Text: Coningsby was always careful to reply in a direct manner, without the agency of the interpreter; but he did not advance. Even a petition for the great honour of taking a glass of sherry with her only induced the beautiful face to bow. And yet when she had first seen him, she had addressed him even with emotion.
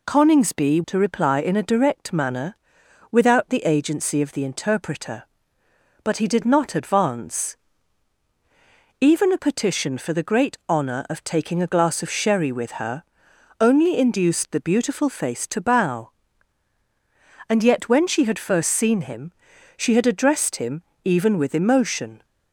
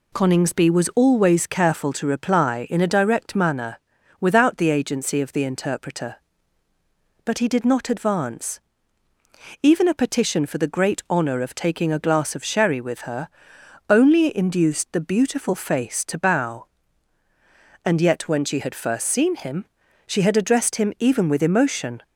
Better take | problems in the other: second | skips "was always careful"; at 0.8 s // pauses between "her" and "only"; noticeable; at 13.0 s; 0.58 s long; noticeable in the second // pauses between "him" and "even"; slight; at 20.8 s; 0.22 s long

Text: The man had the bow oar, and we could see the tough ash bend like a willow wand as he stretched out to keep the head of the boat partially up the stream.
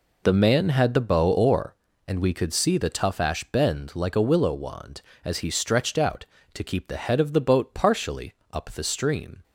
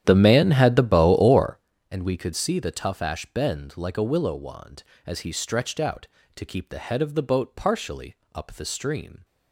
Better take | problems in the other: first | starts louder than the rest; strong; until 1.7 s; 10.5 dB // pauses between "partially" and "up"; slight; at 8.1 s; 0.20 s long; slight in the first

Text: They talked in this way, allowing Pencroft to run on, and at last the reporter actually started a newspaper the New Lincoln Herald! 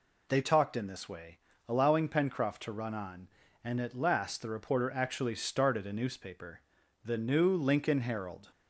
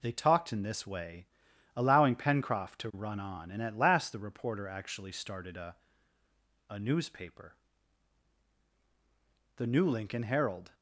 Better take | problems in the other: first | says "a" twice; at 6.6 s // pauses between "newspaper" and "the"; strong; at 7.5 s; 2.0 s long; noticeable in the first

